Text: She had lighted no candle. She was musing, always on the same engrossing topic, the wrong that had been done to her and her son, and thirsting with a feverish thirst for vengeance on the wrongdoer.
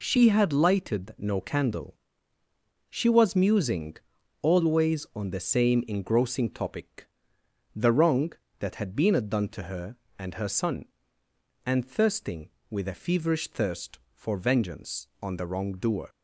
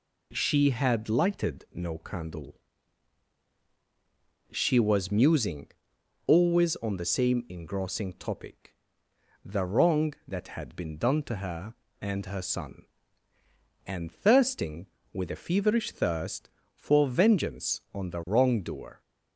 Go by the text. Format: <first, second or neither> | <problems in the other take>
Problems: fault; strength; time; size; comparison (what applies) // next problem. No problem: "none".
neither | none